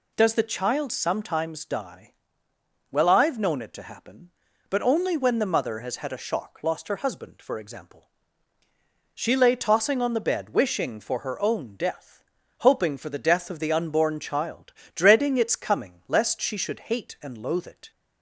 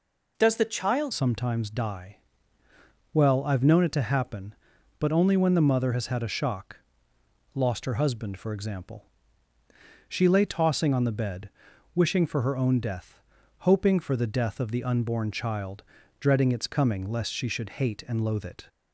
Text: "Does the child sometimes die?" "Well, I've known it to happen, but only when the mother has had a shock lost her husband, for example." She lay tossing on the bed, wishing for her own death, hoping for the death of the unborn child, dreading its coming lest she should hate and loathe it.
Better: first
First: none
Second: changes voice at "sometimes"; from 1.1 s on; 17.5 s long // pauses between "shock" and "lost"; noticeable; at 6.7 s; 0.80 s long

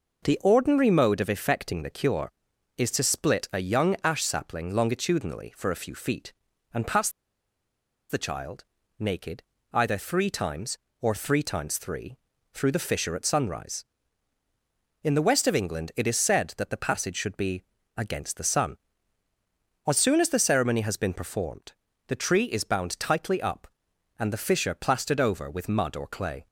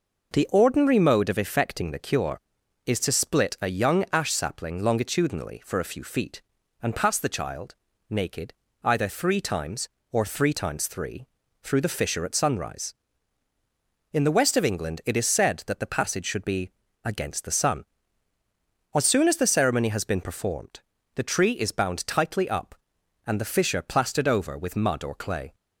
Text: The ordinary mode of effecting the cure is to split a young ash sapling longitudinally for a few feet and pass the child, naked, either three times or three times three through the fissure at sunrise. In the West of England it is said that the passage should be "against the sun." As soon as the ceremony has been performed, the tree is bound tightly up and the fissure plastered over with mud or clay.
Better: second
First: pauses between "pass" and "the"; at 7.0 s; 1.0 s long // pauses between "three" and "through"; slight; at 12.1 s; 0.36 s long // pauses between "be" and "against"; slight; at 17.6 s; 0.36 s long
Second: pauses between "three" and "through"; slight; at 11.2 s; 0.36 s long // pauses between "be" and "against"; slight; at 16.7 s; 0.36 s long

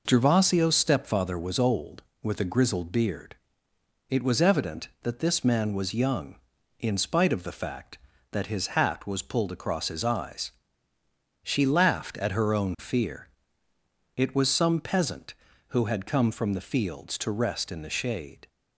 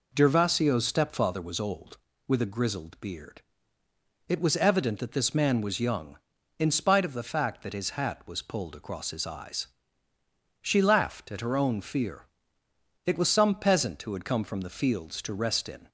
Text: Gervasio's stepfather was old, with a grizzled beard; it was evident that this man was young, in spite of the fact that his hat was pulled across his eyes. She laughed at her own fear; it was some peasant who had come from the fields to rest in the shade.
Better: first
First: none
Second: stops before "the shade"; at 15.8 s

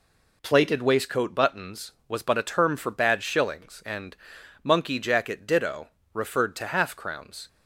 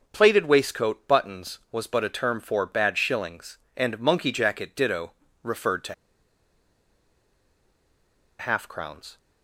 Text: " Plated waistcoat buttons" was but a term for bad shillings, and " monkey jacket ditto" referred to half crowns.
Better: first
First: pauses between "ditto" and "referred"; slight; at 5.8 s; 0.24 s long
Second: pauses between "ditto" and "referred"; slight; at 5.1 s; 0.30 s long // pauses between "to" and "half"; strong; at 5.9 s; 2.4 s long

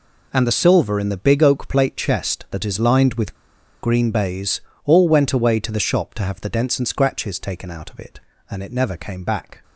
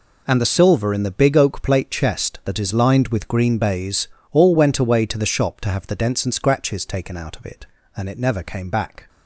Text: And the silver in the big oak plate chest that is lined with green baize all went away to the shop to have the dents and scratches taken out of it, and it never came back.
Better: second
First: pauses between "with" and "green"; noticeable; at 3.3 s; 0.49 s long // pauses between "baize" and "all"; slight; at 4.6 s; 0.24 s long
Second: pauses between "baize" and "all"; slight; at 4.0 s; 0.24 s long

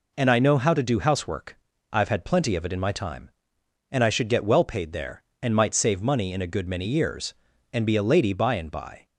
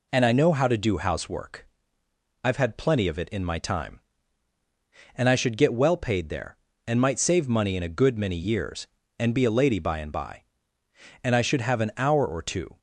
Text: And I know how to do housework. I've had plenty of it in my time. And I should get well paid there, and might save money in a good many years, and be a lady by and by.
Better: first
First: none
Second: goes on to say "And I should have an hour or two"; from 11.2 s on; 1.5 s long

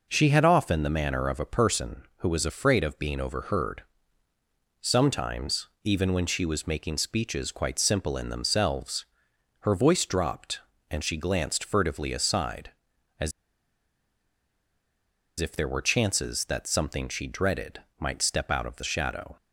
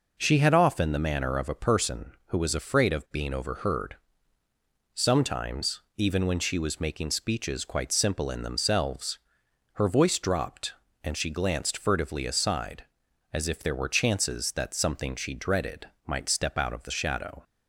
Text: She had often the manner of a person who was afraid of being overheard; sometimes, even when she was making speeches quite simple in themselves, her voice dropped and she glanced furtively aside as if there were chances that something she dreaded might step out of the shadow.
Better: second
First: pauses between "as" and "if"; strong; at 13.3 s; 2.0 s long // pauses between "dreaded" and "might"; slight; at 17.8 s; 0.18 s long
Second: pauses between "dreaded" and "might"; slight; at 15.8 s; 0.18 s long

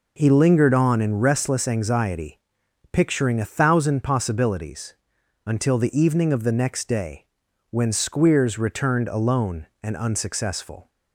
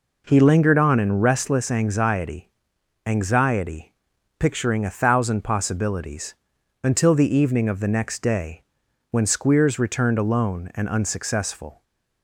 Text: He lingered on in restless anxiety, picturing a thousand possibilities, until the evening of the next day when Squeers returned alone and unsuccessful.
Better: first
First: pauses between "day" and "when"; at 7.2 s; 0.42 s long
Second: says "anxiety" twice; at 3.0 s // pauses between "day" and "when"; noticeable; at 8.6 s; 0.48 s long

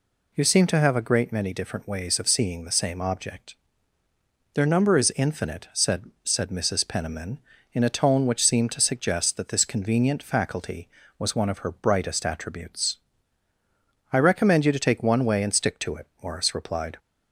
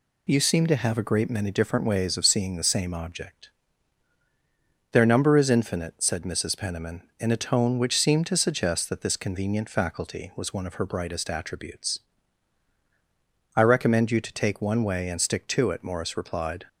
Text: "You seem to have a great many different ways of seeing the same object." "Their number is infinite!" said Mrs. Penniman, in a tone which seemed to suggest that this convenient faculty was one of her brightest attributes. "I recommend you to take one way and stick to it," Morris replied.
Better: second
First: says "said" twice; at 6.2 s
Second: none

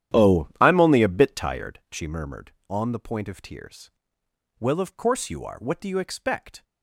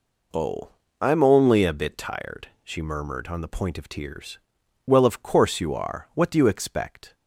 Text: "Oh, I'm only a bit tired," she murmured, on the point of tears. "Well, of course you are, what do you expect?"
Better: second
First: starts louder than the rest; strong; until 1.8 s; 11 dB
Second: none

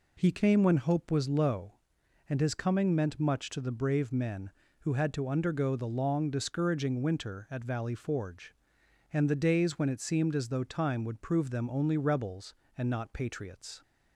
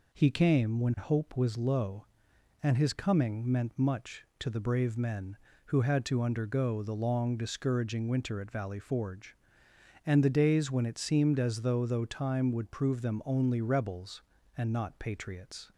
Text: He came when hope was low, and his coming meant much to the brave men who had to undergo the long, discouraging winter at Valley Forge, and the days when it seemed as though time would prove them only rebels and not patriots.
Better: first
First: none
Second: says "though" twice; at 11.8 s

